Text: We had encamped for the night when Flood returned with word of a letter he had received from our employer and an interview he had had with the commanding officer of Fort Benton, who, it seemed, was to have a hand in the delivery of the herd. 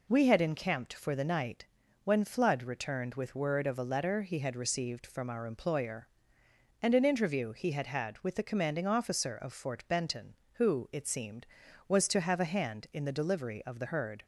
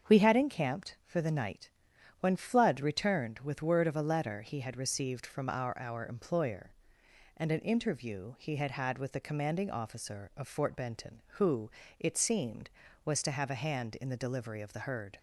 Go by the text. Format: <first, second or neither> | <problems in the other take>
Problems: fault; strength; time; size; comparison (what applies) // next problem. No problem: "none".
first | starts louder than the rest; strong; until 1.1 s; 7 dB // pauses between "night" and "when"; noticeable; at 1.6 s; 0.50 s long; also in the first // says "our" twice; at 5.7 s